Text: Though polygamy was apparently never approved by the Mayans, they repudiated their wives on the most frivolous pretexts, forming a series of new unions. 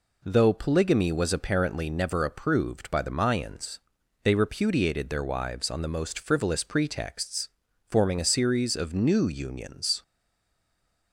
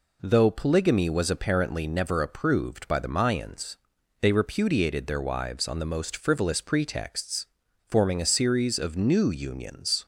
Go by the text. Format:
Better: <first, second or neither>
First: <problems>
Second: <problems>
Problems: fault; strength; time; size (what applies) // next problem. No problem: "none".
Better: second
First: stays silent after the last word; from 10.0 s on; 1.1 s long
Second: none